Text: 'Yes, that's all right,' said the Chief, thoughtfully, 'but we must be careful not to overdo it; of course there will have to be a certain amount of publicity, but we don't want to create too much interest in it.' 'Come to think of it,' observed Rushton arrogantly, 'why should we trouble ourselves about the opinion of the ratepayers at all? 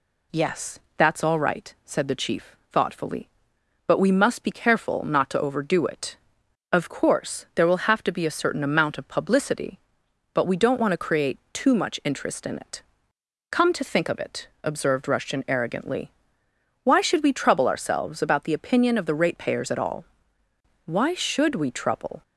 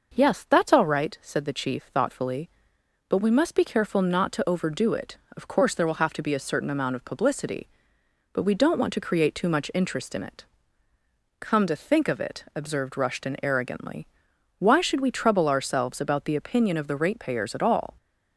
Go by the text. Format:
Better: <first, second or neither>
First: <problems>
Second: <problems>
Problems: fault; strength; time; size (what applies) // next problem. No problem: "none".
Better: second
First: goes on to say "Why should we trouble"; from 20.8 s on; 1.3 s long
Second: none